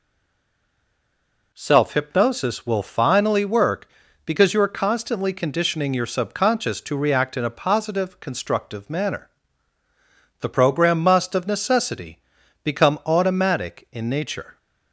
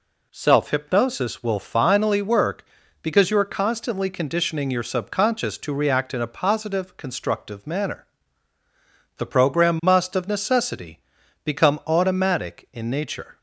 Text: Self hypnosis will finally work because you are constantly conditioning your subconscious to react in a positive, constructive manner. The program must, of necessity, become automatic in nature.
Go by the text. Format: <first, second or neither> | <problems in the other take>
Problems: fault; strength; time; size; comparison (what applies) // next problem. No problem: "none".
second | stays silent before the first word; noticeable; until 1.5 s; 1.5 s long